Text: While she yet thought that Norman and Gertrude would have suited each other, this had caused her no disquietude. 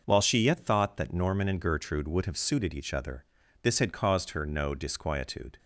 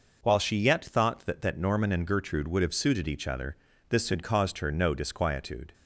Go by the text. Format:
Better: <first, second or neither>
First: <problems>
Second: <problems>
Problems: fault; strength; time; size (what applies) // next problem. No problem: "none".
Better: first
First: none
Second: says "that" twice; at 1.4 s